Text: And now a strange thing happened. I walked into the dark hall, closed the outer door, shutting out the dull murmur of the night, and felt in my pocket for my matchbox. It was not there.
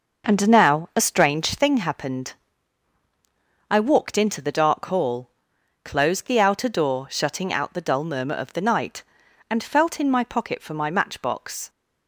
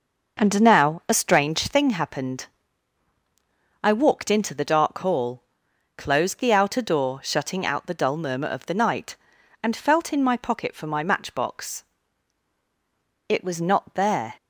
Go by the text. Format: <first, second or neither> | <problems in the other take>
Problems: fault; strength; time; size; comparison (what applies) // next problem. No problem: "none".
second | stops before "It was not there"; at 11.6 s